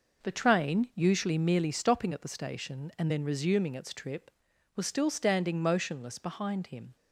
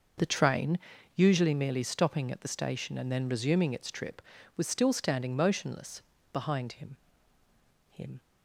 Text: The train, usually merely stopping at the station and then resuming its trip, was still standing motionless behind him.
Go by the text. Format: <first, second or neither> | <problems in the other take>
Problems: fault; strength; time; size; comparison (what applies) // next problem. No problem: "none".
first | pauses between "motionless" and "behind"; slight; at 6.0 s; 0.32 s long // says "him" twice; at 7.9 s